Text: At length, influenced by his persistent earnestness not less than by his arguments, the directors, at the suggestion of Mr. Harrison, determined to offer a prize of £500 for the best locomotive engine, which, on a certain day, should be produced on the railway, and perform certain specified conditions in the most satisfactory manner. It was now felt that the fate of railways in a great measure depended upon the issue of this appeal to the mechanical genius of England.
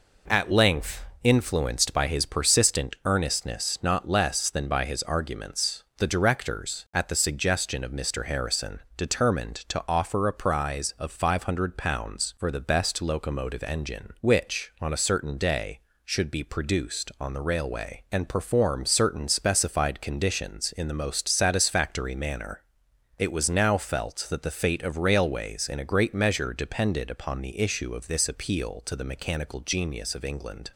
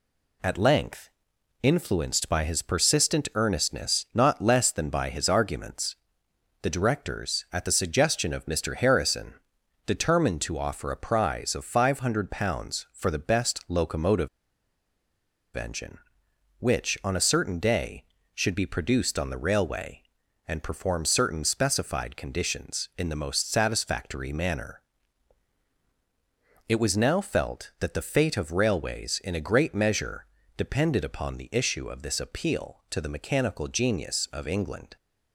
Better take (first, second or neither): first